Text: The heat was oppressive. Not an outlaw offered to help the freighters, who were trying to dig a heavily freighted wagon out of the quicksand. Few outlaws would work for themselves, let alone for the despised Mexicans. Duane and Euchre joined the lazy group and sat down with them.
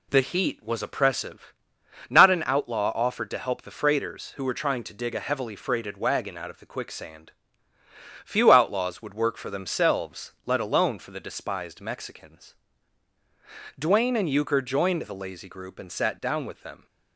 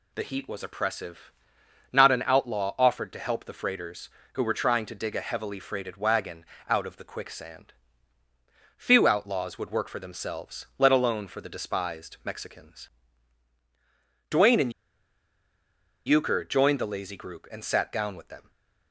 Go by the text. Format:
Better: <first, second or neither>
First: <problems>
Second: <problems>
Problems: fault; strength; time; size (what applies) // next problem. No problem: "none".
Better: first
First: none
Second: pauses between "wagon" and "out"; slight; at 6.4 s; 0.24 s long // pauses between "and" and "Euchre"; strong; at 14.7 s; 1.3 s long // stays silent after the last word; slight; from 18.4 s on; 0.5 s long